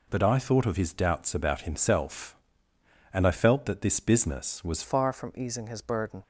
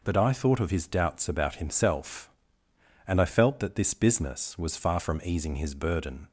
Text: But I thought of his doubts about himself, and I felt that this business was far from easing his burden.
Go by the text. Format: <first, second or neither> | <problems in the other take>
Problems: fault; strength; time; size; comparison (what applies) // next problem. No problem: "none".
second | changes voice at "far"; from 4.8 s on; 1.4 s long